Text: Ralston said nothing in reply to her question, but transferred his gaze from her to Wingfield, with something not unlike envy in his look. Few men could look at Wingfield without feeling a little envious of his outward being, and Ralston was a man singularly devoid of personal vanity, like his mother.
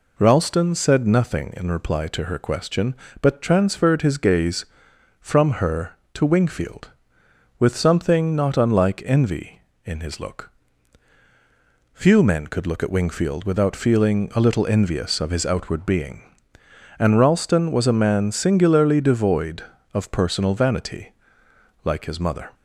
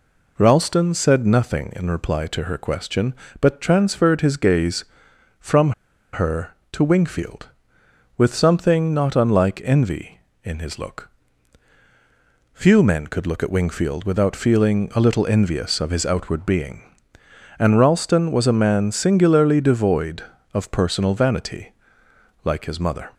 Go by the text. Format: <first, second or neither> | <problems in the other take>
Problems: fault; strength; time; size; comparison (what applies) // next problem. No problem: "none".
first | pauses between "from" and "her"; at 5.7 s; 0.41 s long